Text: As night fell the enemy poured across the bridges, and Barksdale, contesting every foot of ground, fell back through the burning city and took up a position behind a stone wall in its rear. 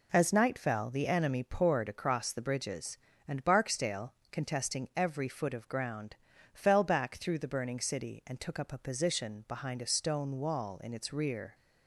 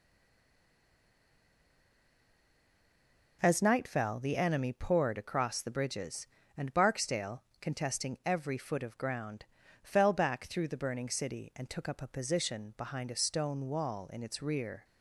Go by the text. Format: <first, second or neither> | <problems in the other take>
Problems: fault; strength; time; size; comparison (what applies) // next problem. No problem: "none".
first | stays silent before the first word; strong; until 3.3 s; 3.3 s long